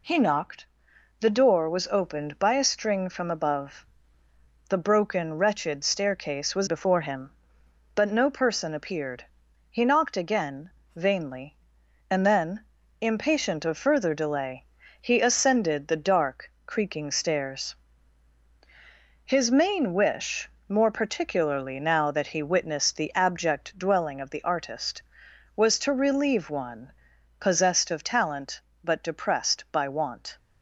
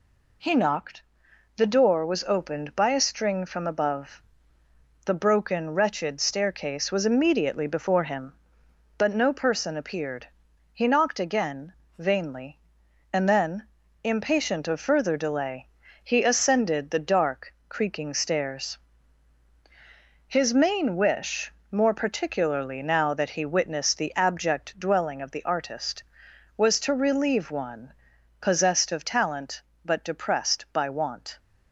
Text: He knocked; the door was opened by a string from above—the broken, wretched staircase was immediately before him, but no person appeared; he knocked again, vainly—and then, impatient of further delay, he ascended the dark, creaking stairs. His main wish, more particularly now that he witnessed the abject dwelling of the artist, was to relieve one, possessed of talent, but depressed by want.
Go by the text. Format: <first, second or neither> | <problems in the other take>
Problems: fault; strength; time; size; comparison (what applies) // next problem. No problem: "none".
second | skips "immediately"; at 6.6 s